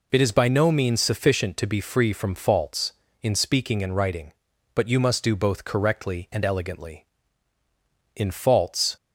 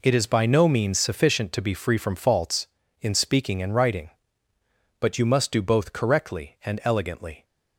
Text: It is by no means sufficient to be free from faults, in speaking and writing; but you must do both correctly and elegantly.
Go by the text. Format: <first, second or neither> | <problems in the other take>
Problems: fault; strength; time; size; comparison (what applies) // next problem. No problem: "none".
second | goes on to say "In faults"; noticeable; from 8.1 s on; 0.80 s long